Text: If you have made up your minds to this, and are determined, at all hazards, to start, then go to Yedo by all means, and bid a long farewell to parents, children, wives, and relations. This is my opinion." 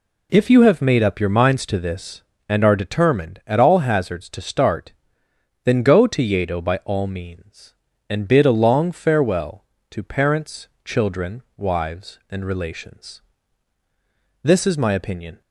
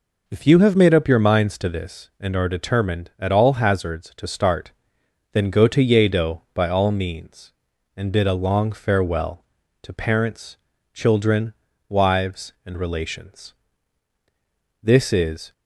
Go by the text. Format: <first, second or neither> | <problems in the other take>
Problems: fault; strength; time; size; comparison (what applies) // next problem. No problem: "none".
first | stops before "my opinion"; at 15.5 s